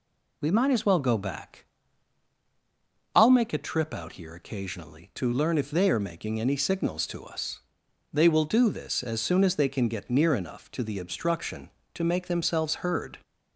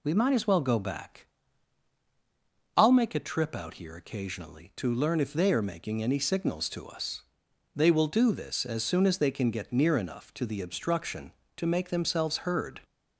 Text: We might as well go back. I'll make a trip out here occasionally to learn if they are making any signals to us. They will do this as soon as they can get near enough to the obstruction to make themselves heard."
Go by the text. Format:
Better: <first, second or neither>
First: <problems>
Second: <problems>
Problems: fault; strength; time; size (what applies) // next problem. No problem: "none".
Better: neither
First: none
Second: none